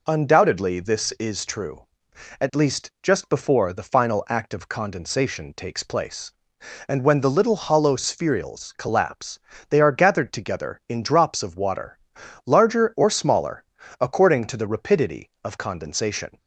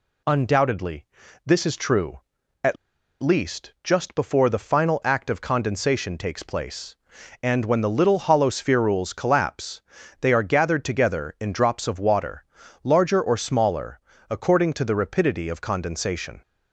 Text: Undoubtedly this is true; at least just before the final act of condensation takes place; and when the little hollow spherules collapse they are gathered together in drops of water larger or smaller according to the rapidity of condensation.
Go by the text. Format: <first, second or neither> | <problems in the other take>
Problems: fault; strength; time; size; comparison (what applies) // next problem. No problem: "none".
first | pauses between "Undoubtedly" and "this"; at 1.0 s; 0.40 s long // pauses between "at" and "least"; noticeable; at 2.7 s; 0.47 s long // pauses between "collapse" and "they"; at 9.7 s; 0.40 s long; slight in the first // pauses between "water" and "larger"; at 12.4 s; 0.40 s long; noticeable in the first // pauses between "smaller" and "according"; slight; at 13.9 s; 0.30 s long; slight in the first